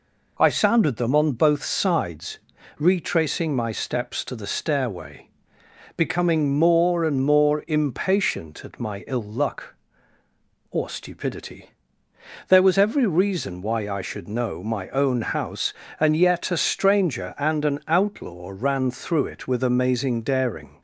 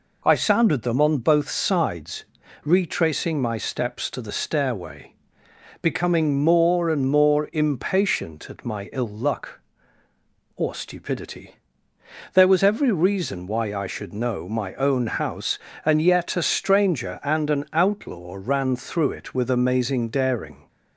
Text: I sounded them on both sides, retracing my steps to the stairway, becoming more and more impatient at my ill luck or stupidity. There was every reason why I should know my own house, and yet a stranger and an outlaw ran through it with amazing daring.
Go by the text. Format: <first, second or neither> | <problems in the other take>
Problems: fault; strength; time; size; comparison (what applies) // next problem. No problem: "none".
neither | none